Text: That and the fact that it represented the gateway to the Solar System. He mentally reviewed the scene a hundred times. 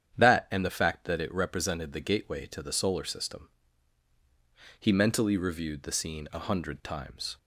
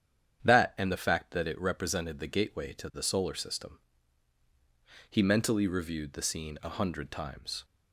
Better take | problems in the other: neither | starts louder than the rest; strong; the same in both

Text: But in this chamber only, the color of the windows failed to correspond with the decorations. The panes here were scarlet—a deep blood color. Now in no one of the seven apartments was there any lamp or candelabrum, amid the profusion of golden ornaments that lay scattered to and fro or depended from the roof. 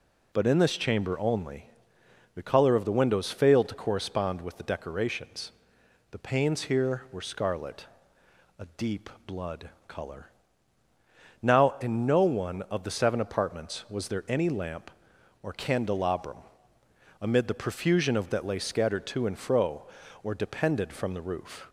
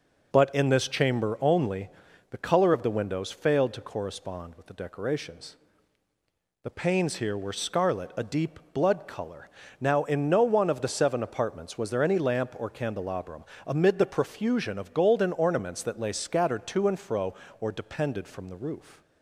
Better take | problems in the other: second | pauses between "deep" and "blood"; slight; at 9.0 s; 0.18 s long // pauses between "blood" and "color"; slight; at 9.6 s; 0.18 s long // skips "golden ornaments"; at 18.3 s

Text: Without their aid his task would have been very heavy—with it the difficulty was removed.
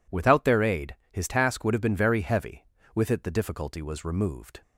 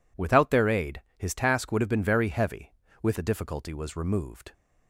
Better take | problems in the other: first | pauses between "aid" and "his"; slight; at 1.0 s; 0.16 s long; slight in the first // skips "it"; at 3.1 s

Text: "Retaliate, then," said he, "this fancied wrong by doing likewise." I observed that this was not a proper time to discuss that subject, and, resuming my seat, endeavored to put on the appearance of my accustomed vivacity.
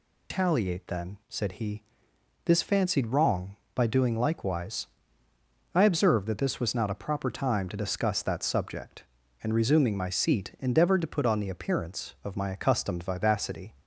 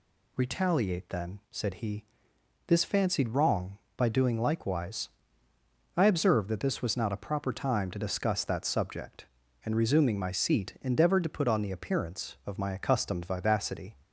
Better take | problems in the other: second | loses the start of "Retaliate"; at 0.3 s; 165 ms

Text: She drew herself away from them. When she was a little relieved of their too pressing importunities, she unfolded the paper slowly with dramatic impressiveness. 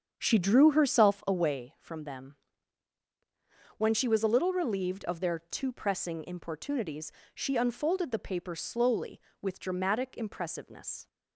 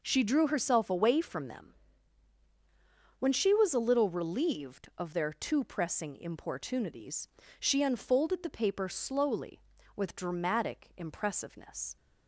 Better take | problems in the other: second | starts louder than the rest; strong; until 1.6 s; 7.5 dB

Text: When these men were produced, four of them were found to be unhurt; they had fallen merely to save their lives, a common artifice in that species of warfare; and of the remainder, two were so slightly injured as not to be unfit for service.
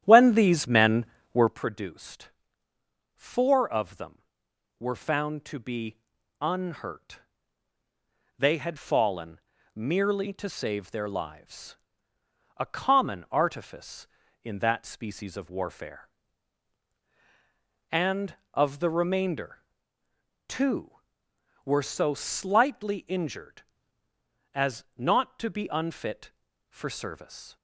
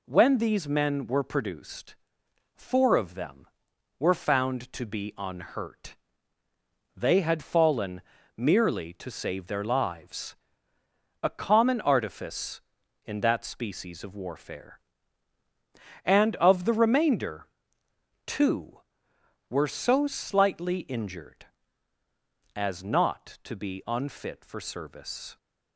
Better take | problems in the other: second | starts louder than the rest; strong; until 1.6 s; 11 dB // pauses between "be" and "unhurt"; at 5.9 s; 0.42 s long // pauses between "fallen" and "merely"; at 9.3 s; 0.38 s long; slight in the second

